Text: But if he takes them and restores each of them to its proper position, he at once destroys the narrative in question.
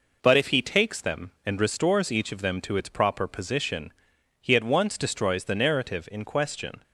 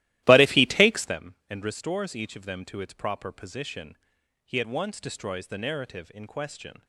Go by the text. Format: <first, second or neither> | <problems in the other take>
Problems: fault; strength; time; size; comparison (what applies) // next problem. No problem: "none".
first | starts louder than the rest; strong; until 1.2 s; 15.5 dB